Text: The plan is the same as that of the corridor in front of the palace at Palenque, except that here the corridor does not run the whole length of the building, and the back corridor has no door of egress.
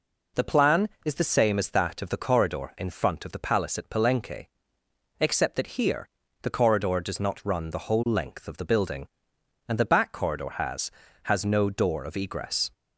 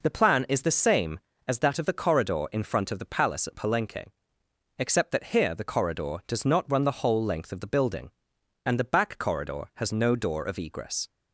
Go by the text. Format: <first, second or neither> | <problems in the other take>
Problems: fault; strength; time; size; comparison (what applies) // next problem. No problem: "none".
second | pauses between "here" and "the"; slight; at 6.0 s; 0.34 s long // says "has" twice; at 11.2 s